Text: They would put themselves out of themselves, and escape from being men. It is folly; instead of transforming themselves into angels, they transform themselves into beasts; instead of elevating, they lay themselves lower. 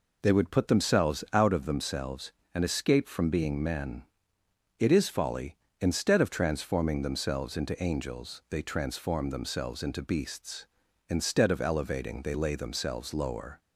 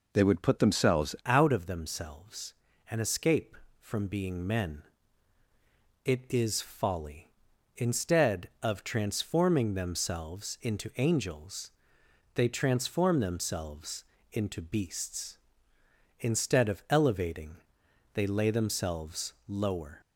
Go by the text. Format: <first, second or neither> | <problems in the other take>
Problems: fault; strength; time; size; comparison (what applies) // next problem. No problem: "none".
first | changes voice at "out"; from 1.2 s on; 18.8 s long // pauses between "themselves" and "into"; slight; at 14.0 s; 0.30 s long